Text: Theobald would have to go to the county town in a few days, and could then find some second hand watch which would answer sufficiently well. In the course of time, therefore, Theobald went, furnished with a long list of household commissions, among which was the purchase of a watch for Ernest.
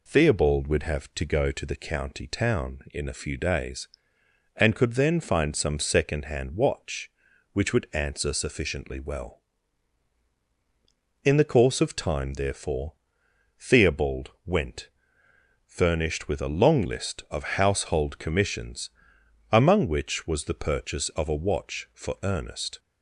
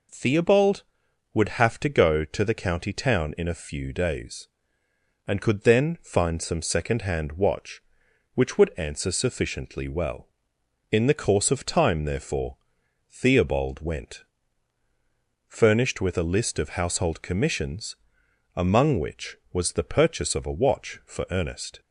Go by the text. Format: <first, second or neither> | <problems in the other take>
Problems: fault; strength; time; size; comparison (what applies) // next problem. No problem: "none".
first | skips "long"; at 16.2 s